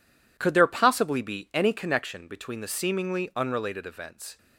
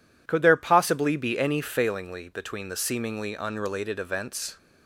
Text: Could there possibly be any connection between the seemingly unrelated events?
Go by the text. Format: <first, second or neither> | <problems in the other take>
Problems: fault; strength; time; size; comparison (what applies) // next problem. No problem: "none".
first | says "failingly" for "connection"; at 1.6 s